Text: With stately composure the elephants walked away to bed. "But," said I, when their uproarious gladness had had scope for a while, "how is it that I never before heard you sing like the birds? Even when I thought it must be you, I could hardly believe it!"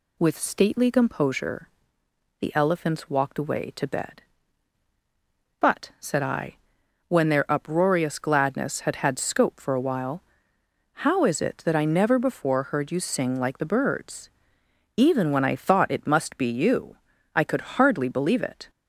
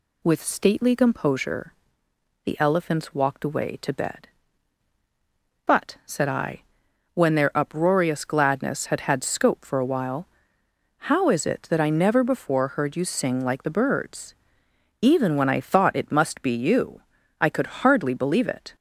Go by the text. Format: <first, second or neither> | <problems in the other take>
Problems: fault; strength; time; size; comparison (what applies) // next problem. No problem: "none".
neither | pauses between "composure" and "the"; noticeable; the same in both